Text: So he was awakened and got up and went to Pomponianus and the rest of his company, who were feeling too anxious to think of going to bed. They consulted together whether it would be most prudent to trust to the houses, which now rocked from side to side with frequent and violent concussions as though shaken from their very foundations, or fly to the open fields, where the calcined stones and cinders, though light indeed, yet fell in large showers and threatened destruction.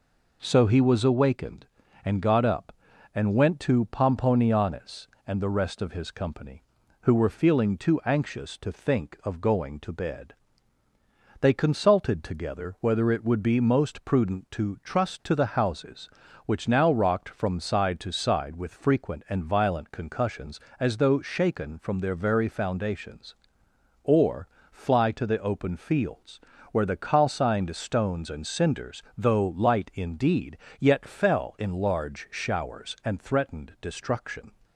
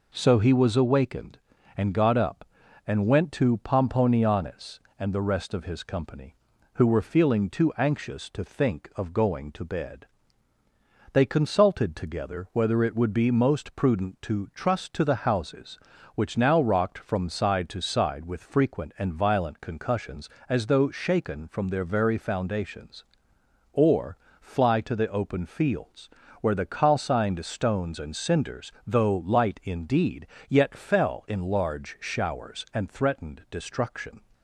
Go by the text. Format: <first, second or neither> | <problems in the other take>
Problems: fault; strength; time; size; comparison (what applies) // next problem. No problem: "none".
neither | pauses between "or" and "fly"; slight; the same in both